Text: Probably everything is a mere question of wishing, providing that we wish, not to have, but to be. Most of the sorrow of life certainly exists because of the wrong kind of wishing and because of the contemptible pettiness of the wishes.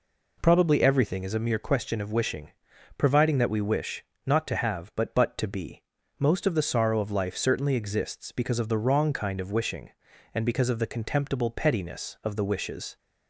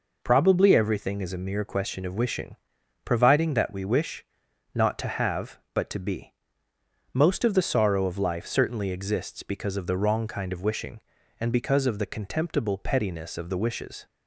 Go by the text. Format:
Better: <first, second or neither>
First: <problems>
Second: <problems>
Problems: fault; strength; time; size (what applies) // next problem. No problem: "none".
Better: second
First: says "but" twice; at 5.1 s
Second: none